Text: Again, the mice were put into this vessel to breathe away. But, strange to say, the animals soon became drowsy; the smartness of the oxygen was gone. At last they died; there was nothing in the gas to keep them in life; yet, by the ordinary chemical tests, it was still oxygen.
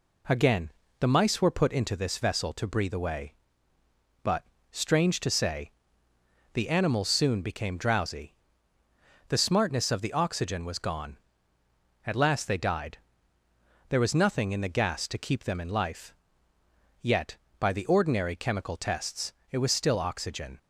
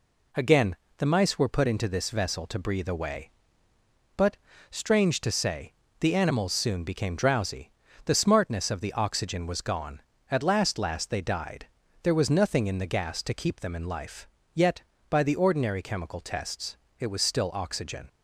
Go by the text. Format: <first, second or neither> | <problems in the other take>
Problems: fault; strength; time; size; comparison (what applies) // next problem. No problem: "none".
first | says "last" twice; at 10.7 s